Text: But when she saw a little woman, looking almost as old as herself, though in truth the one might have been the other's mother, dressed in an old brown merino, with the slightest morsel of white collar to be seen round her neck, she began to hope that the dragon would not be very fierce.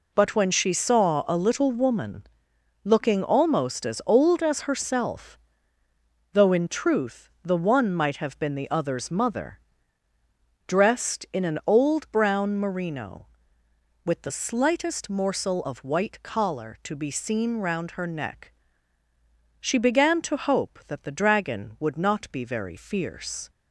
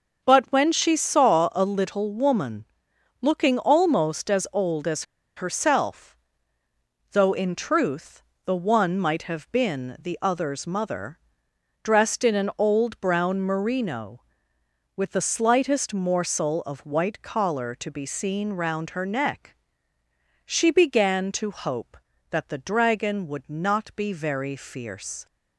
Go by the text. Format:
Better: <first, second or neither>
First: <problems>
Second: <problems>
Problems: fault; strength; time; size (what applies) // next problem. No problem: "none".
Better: first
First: none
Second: starts louder than the rest; noticeable; until 1.2 s; 6 dB // pauses between "as" and "herself"; slight; at 5.0 s; 0.32 s long // pauses between "truth" and "the"; slight; at 8.2 s; 0.24 s long